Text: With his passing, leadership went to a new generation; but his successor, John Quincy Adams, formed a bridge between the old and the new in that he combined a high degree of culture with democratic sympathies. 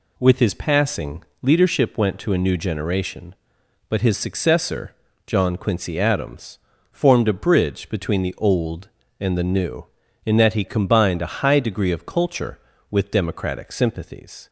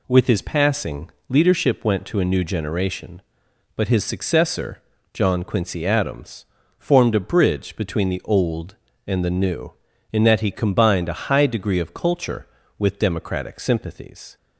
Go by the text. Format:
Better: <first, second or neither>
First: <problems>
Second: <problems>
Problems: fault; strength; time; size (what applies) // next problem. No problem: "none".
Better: neither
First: none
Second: none